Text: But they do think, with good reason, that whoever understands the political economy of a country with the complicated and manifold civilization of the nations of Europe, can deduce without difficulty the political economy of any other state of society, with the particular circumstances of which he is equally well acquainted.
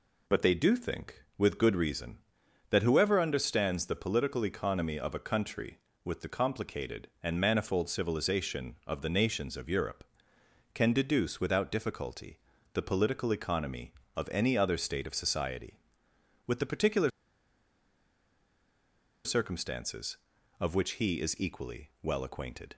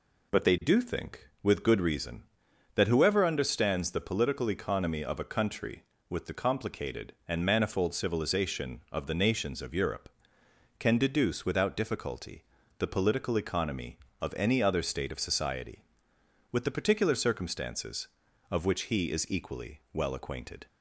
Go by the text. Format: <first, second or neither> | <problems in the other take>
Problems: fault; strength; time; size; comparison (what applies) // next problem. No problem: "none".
second | pauses between "difficulty" and "the"; slight; at 12.3 s; 0.36 s long; slight in the second // pauses between "particular" and "circumstances"; strong; at 17.0 s; 2.1 s long